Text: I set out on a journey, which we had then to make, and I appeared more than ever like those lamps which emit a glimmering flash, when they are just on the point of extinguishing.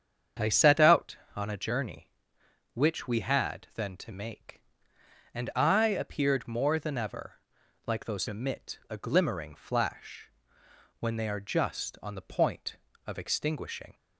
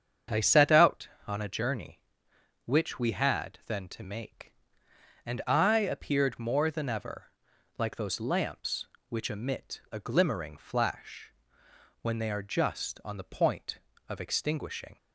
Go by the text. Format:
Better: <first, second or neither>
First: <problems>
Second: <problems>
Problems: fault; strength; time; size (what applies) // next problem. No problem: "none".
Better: second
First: starts louder than the rest; strong; until 1.5 s; 7.5 dB // pauses between "ever" and "like"; noticeable; at 7.3 s; 0.48 s long // skips "lamps which"; at 8.2 s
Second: starts louder than the rest; strong; until 1.5 s; 7.5 dB // pauses between "ever" and "like"; noticeable; at 7.3 s; 0.48 s long